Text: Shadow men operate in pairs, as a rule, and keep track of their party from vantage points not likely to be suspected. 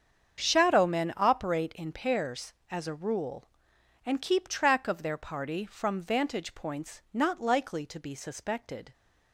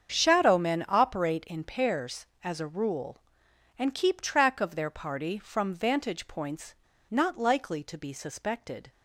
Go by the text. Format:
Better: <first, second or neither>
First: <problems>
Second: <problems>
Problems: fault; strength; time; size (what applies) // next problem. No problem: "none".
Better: first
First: starts louder than the rest; strong; until 1.4 s; 7.5 dB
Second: starts louder than the rest; strong; until 1.1 s; 7.5 dB // pauses between "points" and "not"; slight; at 6.7 s; 0.34 s long